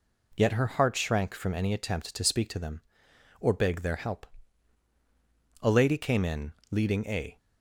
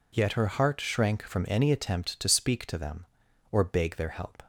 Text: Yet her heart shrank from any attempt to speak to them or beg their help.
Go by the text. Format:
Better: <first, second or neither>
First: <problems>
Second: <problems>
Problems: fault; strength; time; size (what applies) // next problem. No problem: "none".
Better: second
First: goes on to say "A lady came in leading a"; strong; from 5.6 s on; 1.7 s long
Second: none